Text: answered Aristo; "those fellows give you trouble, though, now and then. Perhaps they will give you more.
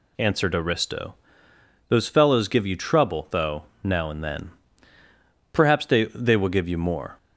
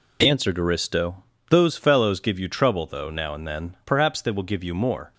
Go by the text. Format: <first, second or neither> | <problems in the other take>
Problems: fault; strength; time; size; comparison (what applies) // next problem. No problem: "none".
second | says "they" twice; at 6.0 s